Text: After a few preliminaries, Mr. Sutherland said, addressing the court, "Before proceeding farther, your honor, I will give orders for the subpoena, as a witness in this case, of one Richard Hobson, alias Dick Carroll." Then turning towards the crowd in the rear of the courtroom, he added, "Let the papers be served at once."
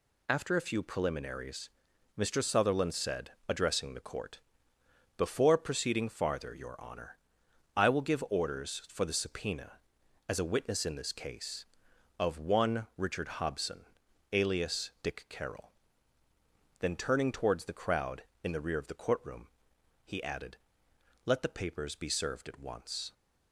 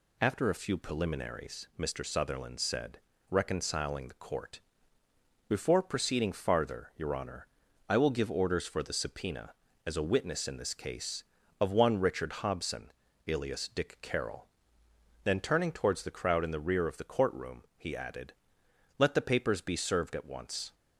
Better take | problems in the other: first | says "reconciling" for "addressing"; at 3.2 s

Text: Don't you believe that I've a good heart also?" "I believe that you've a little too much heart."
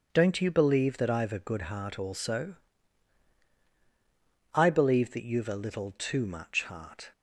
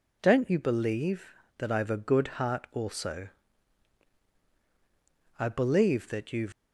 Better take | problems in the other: first | stops before "a little too much heart"; at 6.5 s

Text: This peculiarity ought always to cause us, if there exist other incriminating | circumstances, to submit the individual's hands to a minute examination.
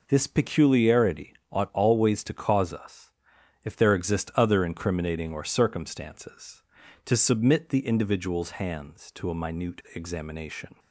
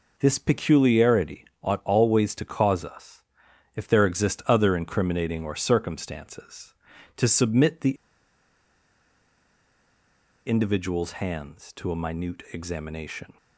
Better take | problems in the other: first | pauses between "peculiarity" and "ought"; slight; at 1.4 s; 0.18 s long; slight in the first // pauses between "the" and "individual's"; strong; at 7.9 s; 2.5 s long

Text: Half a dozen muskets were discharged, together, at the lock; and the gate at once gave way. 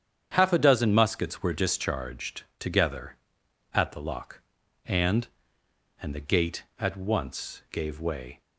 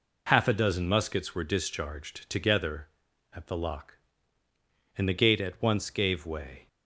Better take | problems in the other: second | starts louder than the rest; strong; until 1.3 s; 8.5 dB // says "and" twice; at 6.0 s

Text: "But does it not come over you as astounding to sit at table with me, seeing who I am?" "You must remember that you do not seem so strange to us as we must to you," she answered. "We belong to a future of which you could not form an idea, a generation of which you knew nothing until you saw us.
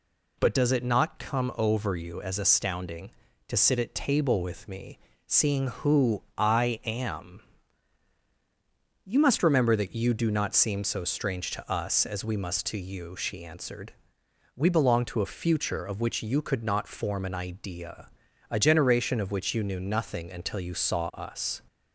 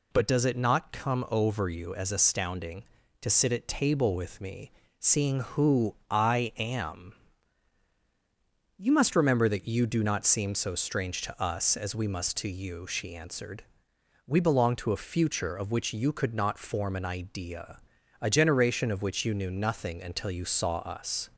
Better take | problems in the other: neither | none

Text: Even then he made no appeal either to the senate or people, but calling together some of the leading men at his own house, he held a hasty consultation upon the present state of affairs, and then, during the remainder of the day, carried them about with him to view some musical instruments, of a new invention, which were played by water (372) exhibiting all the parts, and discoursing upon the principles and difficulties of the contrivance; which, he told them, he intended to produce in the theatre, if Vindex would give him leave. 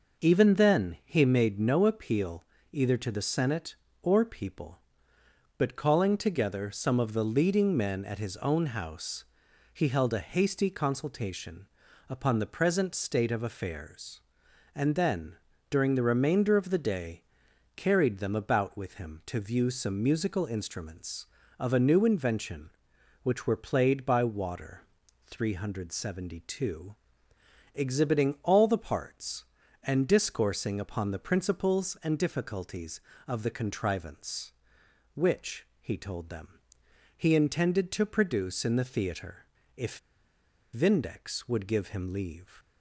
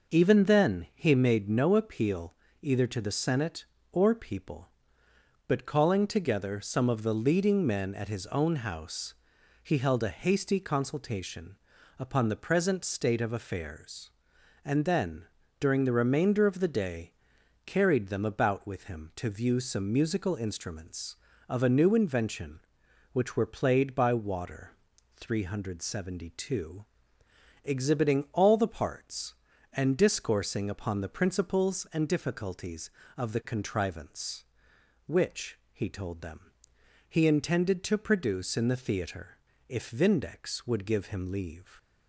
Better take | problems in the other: second | pauses between "appeal" and "either"; slight; at 2.4 s; 0.28 s long; slight in the second // pauses between "consultation" and "upon"; at 11.6 s; 0.44 s long; also in the second // pauses between "if" and "Vindex"; noticeable; at 39.9 s; 0.75 s long

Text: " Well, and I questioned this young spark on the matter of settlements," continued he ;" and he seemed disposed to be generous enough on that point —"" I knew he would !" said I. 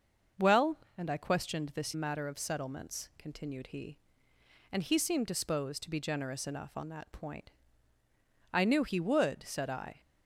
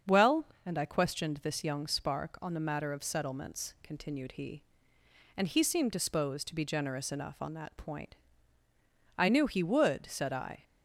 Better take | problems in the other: second | starts louder than the rest; until 1.5 s; 6.5 dB; strong in the second // skips "young spark on the"; at 1.9 s

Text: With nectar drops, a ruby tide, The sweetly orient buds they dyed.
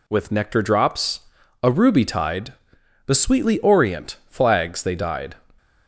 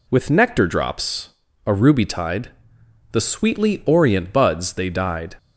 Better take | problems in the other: second | says "flags" for "buds"; at 4.2 s

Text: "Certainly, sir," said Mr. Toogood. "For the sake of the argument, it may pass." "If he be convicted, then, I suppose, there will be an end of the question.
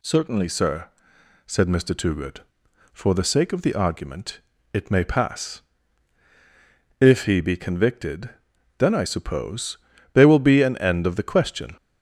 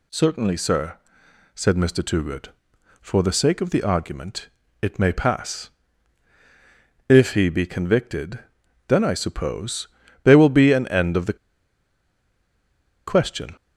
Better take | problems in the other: first | pauses between "the" and "question"; strong; at 11.3 s; 1.7 s long

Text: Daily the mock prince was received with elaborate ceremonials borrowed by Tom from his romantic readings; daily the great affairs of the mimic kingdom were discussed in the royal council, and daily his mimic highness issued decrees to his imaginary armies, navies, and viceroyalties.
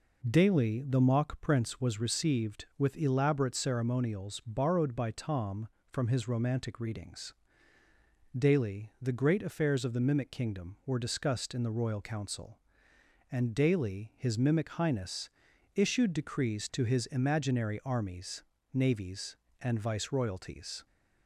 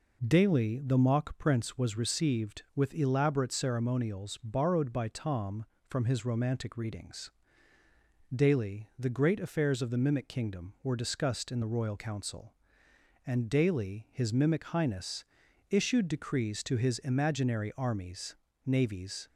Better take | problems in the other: first | pauses between "highness" and "issued"; noticeable; at 15.2 s; 0.46 s long; noticeable in the first // stops before "and viceroyalties"; at 19.2 s

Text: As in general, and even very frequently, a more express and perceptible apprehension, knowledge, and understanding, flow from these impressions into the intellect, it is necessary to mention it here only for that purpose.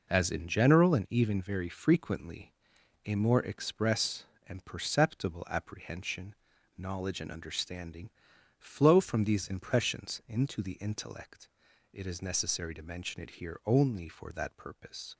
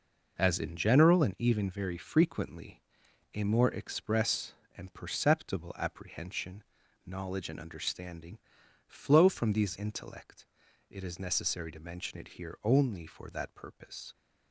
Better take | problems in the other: first | skips "impressions into the"; at 9.7 s

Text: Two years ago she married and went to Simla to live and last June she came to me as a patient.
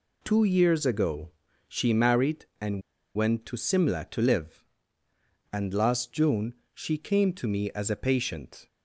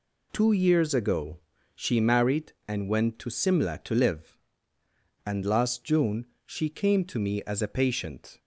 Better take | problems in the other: second | pauses between "ago" and "she"; slight; at 1.3 s; 0.36 s long; slight in the second // pauses between "and" and "went"; slight; at 2.8 s; 0.33 s long // pauses between "June" and "she"; slight; at 6.5 s; 0.20 s long; slight in the second

